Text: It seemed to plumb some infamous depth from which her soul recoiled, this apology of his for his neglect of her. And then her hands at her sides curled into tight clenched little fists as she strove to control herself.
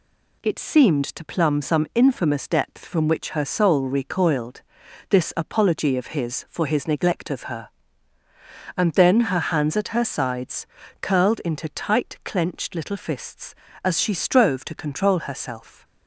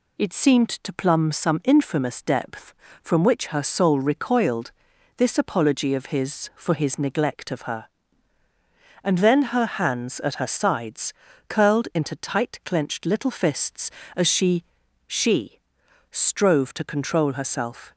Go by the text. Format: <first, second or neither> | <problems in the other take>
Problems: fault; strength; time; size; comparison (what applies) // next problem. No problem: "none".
first | pauses between "sides" and "curled"; slight; at 11.1 s; 0.34 s long; slight in the first // says "she" twice; at 15.0 s